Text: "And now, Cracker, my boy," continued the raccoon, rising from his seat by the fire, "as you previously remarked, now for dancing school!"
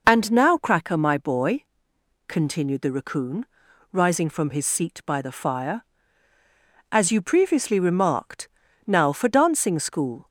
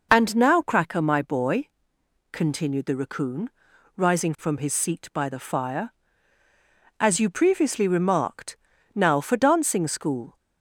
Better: neither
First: none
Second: none

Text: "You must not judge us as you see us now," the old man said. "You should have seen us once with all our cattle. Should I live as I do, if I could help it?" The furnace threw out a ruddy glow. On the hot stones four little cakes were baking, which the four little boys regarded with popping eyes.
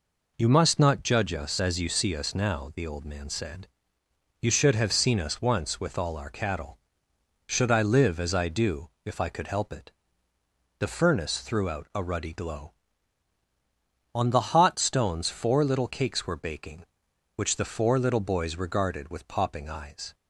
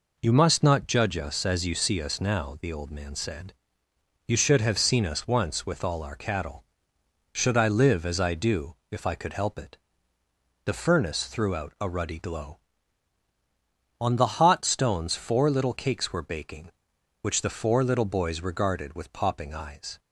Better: neither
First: none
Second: none

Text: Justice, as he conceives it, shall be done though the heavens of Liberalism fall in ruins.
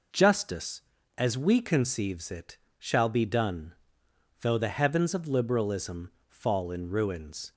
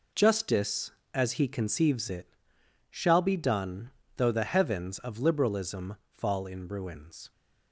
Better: second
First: says "we" for "he"; at 1.3 s // pauses between "done" and "though"; noticeable; at 3.7 s; 0.68 s long // pauses between "Liberalism" and "fall"; slight; at 6.0 s; 0.22 s long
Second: pauses between "done" and "though"; slight; at 3.8 s; 0.28 s long

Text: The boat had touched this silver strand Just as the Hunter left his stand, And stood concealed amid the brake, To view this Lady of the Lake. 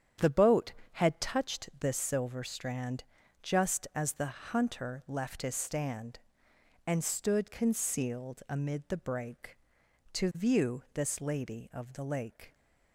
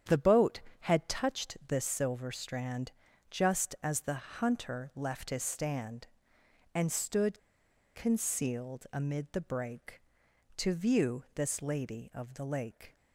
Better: first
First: starts louder than the rest; strong; until 1.4 s; 9 dB // pauses between "strand" and "Just"; at 3.0 s; 0.38 s long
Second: starts louder than the rest; strong; until 1.2 s; 8.5 dB // pauses between "strand" and "Just"; at 2.9 s; 0.38 s long // pauses between "stood" and "concealed"; noticeable; at 7.3 s; 0.58 s long

